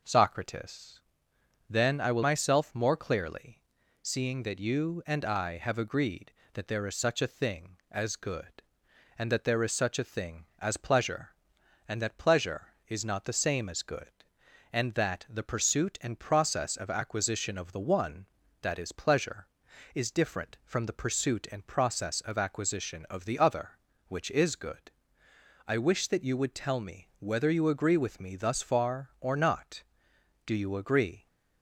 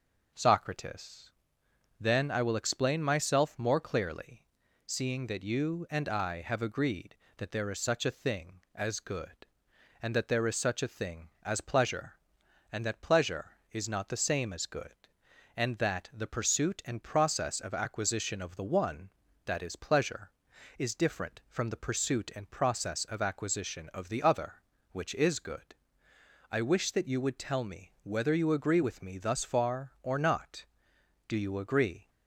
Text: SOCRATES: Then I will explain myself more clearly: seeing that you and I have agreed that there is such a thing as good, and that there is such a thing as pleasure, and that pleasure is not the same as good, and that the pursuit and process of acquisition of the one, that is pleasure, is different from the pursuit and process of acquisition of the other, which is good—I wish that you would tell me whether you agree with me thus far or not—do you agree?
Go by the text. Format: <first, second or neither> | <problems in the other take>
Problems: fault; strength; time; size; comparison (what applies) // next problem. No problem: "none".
second | skips "explain"; at 2.2 s